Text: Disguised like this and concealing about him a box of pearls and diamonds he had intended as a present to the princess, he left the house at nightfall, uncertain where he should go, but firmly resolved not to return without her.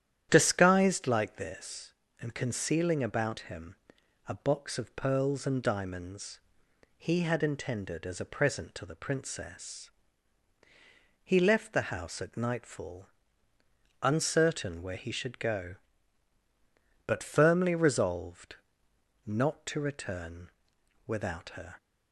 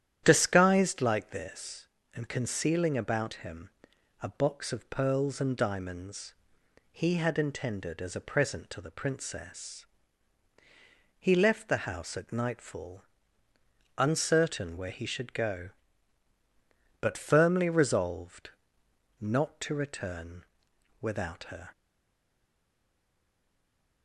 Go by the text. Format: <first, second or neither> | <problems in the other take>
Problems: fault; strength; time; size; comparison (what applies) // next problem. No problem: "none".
first | starts louder than the rest; strong; until 1.2 s; 10.5 dB; strong in the first // pauses between "him" and "a"; noticeable; at 3.6 s; 0.54 s long; noticeable in the first // pauses between "diamonds" and "he"; noticeable; at 6.3 s; 0.58 s long; noticeable in the first // pauses between "resolved" and "not"; noticeable; at 18.5 s; 0.68 s long; noticeable in the first // pauses between "return" and "without"; noticeable; at 20.4 s; 0.56 s long; noticeable in the first // stays silent after the last word; from 21.7 s on; 2.3 s long